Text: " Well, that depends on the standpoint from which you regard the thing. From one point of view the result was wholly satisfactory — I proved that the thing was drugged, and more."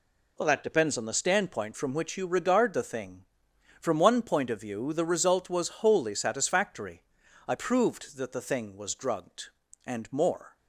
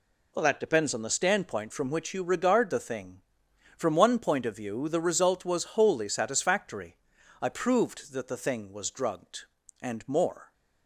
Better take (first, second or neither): neither